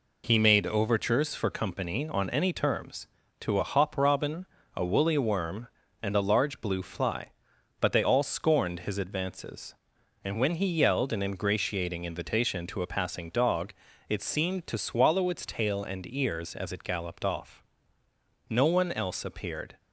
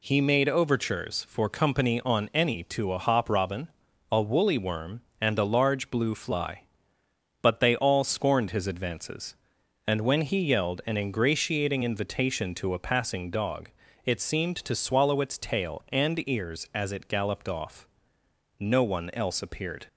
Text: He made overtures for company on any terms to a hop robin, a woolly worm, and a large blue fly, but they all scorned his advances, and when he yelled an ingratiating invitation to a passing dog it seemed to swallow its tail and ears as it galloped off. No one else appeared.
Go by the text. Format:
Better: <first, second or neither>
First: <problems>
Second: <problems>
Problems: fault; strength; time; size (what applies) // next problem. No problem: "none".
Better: first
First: pauses between "dog" and "it"; slight; at 13.7 s; 0.36 s long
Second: skips "terms"; at 2.6 s // pauses between "dog" and "it"; slight; at 13.6 s; 0.34 s long